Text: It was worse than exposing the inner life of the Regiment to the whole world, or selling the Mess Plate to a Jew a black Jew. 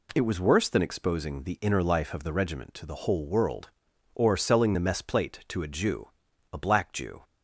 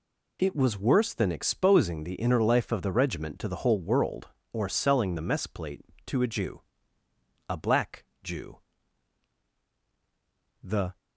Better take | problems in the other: first | pauses between "Jew" and "a"; noticeable; at 6.6 s; 0.88 s long; also in the first // pauses between "black" and "Jew"; slight; at 8.0 s; 0.18 s long // goes on to say "The"; slight; from 10.6 s on; 0.36 s long

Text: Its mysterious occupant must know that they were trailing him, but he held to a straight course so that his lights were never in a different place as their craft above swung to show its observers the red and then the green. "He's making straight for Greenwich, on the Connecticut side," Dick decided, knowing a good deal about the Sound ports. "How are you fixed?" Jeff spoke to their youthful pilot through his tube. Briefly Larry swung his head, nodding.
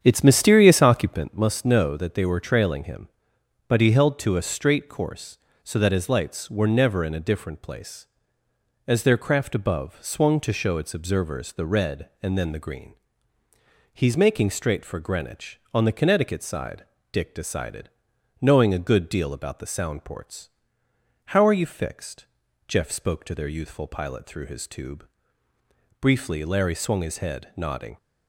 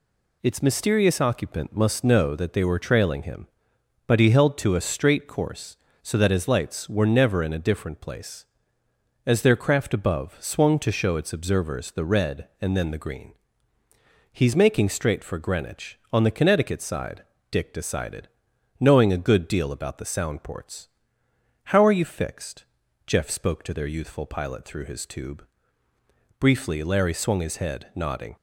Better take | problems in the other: second | starts louder than the rest; strong; until 1.2 s; 8.5 dB

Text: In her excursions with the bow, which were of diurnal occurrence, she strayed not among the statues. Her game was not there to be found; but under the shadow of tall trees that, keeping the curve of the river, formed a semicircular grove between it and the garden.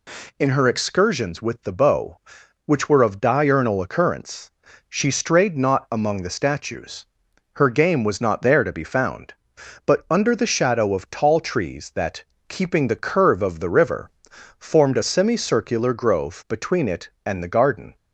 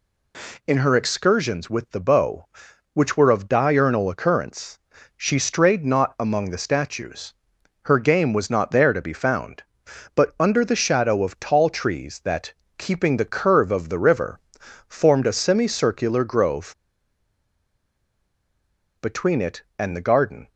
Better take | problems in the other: first | pauses between "grove" and "between"; strong; at 16.7 s; 2.2 s long

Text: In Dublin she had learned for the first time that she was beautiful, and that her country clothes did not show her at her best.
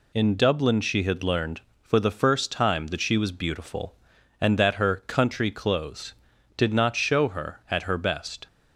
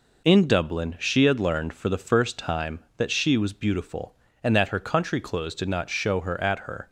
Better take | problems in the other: first | stops before "best"; at 6.8 s

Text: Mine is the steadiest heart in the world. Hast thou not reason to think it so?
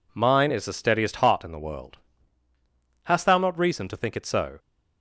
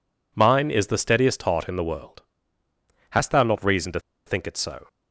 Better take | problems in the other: first | pauses between "to" and "think"; slight; at 4.0 s; 0.25 s long

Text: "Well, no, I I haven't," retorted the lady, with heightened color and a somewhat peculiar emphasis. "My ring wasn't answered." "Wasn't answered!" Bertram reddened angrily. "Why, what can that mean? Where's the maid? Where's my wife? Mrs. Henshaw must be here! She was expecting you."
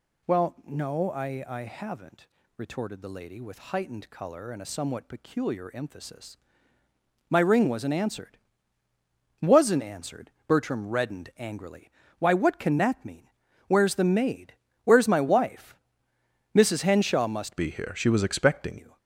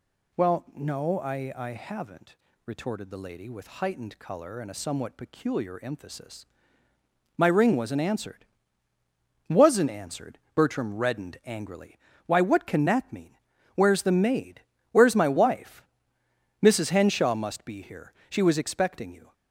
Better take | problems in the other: second | changes voice from "be" to "expecting"; from 17.5 to 18.7 s; 1.2 s long

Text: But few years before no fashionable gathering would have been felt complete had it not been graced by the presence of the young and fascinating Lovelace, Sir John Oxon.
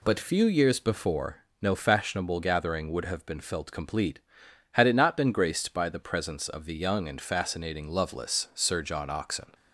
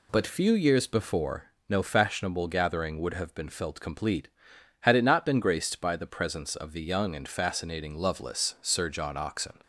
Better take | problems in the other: neither | pauses between "before" and "no"; slight; the same in both

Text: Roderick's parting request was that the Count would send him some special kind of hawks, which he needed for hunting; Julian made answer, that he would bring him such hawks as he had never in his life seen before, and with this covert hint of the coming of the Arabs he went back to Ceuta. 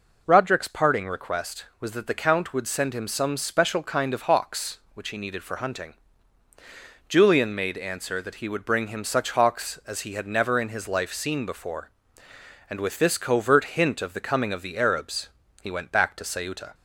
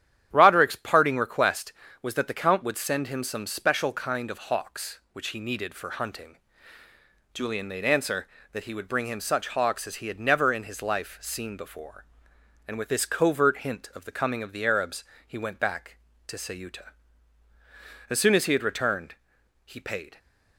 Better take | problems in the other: first | starts louder than the rest; strong; until 1.3 s; 10.5 dB // pauses between "Arabs" and "he"; slight; at 15.0 s; 0.24 s long; slight in the first // goes on to say "As soon as he had returned he paid"; strong; from 18.0 s on; 2.1 s long

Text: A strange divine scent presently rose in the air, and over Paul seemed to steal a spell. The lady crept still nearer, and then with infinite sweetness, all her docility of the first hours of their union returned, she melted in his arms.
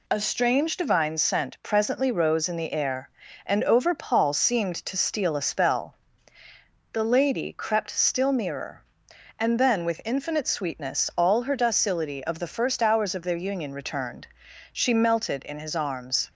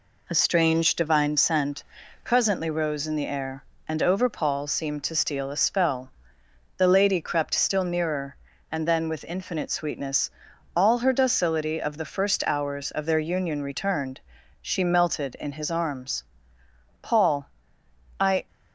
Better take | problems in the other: first | pauses between "scent" and "presently"; at 1.8 s; 0.40 s long // goes on to say "Paul I"; from 17.0 s on; 1.4 s long

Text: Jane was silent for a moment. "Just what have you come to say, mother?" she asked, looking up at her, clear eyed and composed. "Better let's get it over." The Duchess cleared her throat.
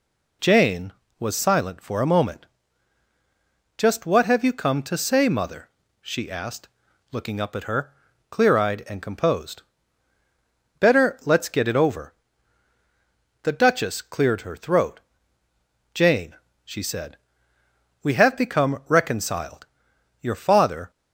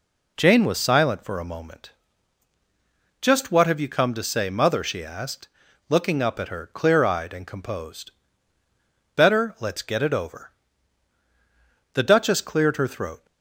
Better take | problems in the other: second | goes on to say "Jane she said we have become reconciled your father"; strong; from 15.9 s on; 4.9 s long

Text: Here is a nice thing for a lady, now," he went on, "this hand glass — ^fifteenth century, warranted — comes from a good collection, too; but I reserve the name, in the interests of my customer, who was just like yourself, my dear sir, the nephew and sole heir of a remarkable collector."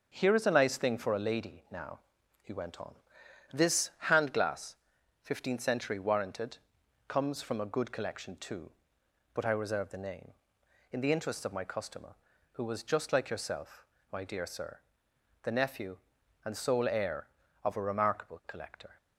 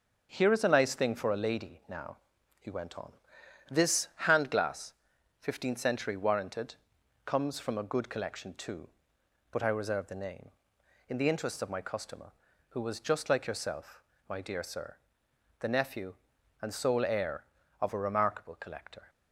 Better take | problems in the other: neither | starts louder than the rest; the same in both

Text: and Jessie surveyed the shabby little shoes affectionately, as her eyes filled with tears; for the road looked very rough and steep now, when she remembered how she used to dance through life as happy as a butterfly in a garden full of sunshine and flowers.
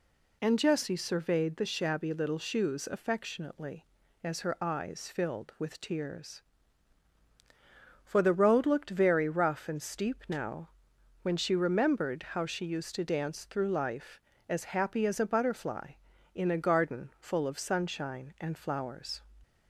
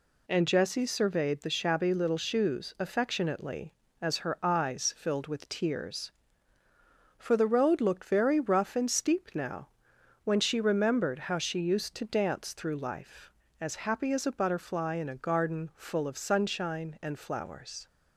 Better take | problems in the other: neither | none

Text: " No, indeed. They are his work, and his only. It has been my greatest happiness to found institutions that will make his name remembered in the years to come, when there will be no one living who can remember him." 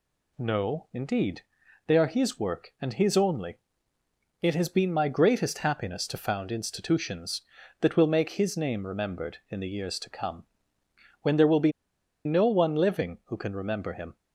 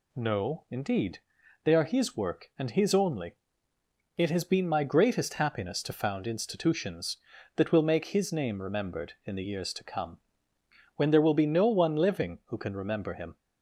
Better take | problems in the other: second | pauses between "be" and "no"; noticeable; at 11.7 s; 0.54 s long

